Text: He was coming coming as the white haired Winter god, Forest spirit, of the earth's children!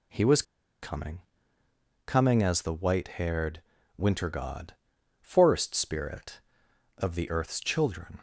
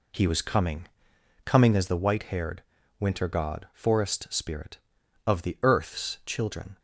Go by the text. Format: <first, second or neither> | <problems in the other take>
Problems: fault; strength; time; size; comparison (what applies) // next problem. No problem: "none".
second | pauses between "was" and "coming"; at 0.4 s; 0.40 s long // pauses between "coming" and "coming"; noticeable; at 1.1 s; 0.86 s long; noticeable in the second // pauses between "haired" and "Winter"; at 3.5 s; 0.38 s long; slight in the second